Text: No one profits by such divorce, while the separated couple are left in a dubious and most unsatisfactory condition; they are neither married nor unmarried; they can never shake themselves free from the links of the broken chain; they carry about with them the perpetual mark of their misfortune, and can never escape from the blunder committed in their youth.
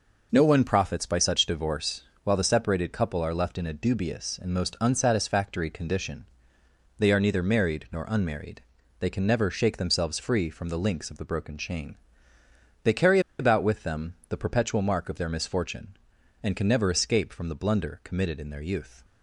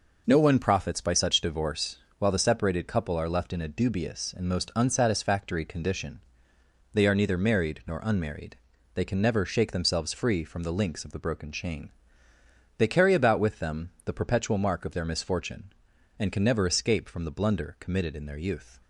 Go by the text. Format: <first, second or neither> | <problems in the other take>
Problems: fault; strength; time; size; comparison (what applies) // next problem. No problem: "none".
second | pauses between "carry" and "about"; slight; at 13.1 s; 0.19 s long // pauses between "them" and "the"; slight; at 14.1 s; 0.16 s long; slight in the second